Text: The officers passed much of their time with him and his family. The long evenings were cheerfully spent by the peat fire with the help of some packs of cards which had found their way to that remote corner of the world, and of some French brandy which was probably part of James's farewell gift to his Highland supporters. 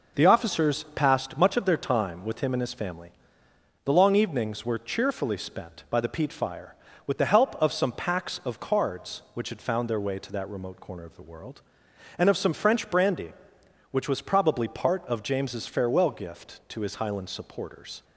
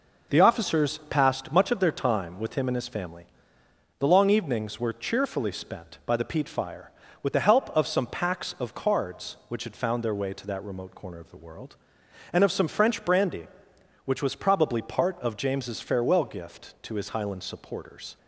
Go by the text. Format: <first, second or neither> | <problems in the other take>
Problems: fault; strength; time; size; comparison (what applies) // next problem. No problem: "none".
neither | none